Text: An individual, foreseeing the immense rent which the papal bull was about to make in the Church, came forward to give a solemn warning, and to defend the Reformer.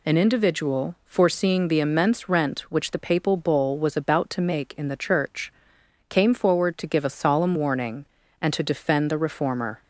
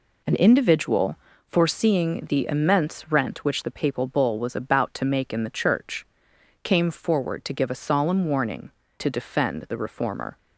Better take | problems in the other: first | skips "and"; at 8.8 s

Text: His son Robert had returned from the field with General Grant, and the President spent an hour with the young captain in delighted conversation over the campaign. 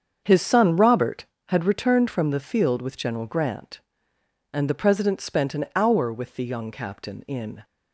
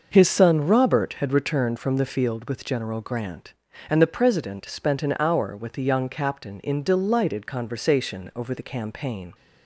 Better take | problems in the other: second | starts louder than the rest; strong; until 1.2 s; 7 dB // stops before "delighted conversation over the campaign"; at 7.6 s

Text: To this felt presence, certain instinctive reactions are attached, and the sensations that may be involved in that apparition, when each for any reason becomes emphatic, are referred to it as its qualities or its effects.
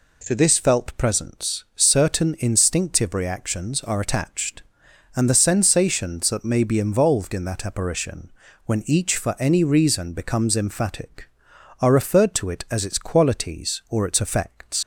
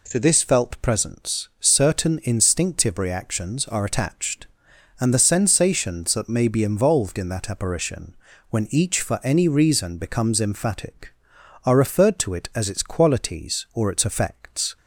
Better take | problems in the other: second | leaves "effects" unfinished; at 14.8 s; 90 ms

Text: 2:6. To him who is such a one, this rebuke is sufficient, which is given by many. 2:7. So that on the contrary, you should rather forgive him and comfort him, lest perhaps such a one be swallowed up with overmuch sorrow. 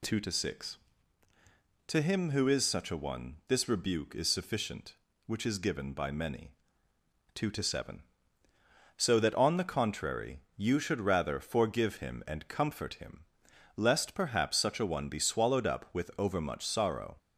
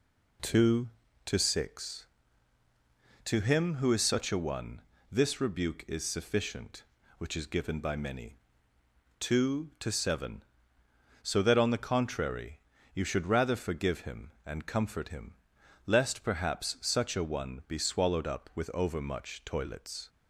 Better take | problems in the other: first | says "toilets" for "sorrow"; at 19.4 s

